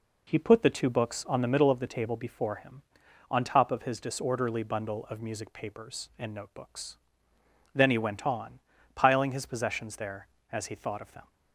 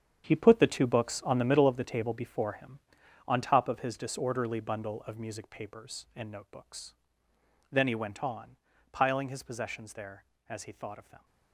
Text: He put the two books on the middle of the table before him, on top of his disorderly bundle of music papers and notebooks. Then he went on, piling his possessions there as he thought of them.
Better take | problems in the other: first | gets quieter; strong; throughout; 12 dB

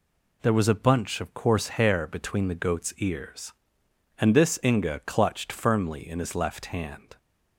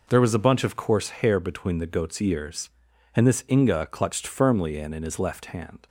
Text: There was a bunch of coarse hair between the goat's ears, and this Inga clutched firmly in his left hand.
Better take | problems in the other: first | says "in" twice; at 4.9 s

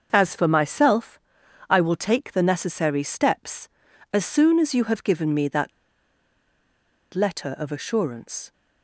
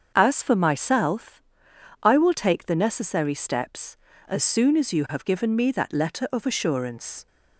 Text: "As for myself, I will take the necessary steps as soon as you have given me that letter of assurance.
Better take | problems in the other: second | starts louder than the rest; until 1.1 s; 6.5 dB; also in the second // pauses between "that" and "letter"; strong; at 5.7 s; 1.4 s long

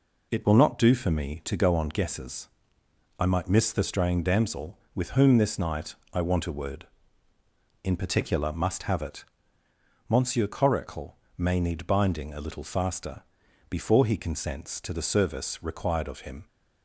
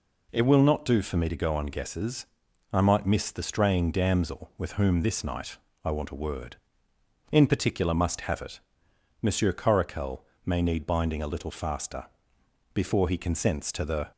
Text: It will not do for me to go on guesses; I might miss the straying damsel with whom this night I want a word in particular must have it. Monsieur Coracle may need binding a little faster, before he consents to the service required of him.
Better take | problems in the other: first | pauses between "night" and "I"; slight; at 5.5 s; 0.26 s long; slight in the first // pauses between "Coracle" and "may"; slight; at 10.2 s; 0.22 s long; slight in the first // stops before "service required of him"; at 14.1 s

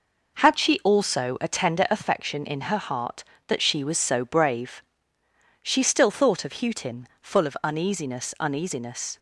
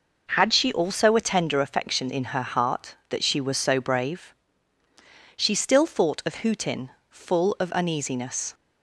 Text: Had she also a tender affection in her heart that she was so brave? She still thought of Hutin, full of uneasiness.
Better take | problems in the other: second | says "uneasiness" twice; at 8.4 s

